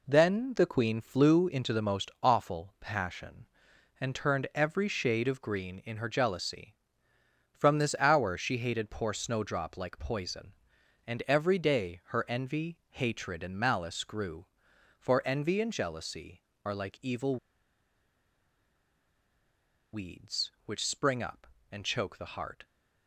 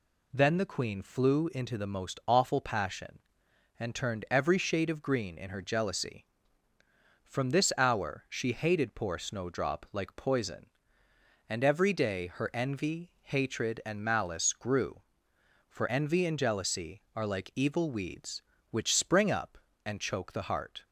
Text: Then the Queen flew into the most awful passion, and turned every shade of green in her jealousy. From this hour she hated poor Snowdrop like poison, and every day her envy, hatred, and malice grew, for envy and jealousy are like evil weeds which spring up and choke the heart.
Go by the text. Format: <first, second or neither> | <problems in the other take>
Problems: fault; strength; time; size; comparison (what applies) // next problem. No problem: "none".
second | pauses between "evil" and "weeds"; strong; at 17.3 s; 2.5 s long